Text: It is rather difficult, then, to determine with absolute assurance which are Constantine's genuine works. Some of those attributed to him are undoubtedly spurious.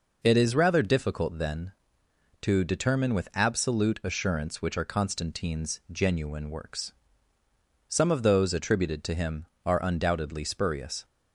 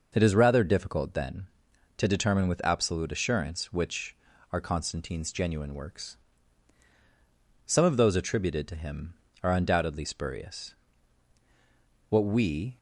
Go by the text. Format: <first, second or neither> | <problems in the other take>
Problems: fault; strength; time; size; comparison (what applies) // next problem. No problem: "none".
first | goes on to say "What we"; noticeable; from 12.0 s on; 0.68 s long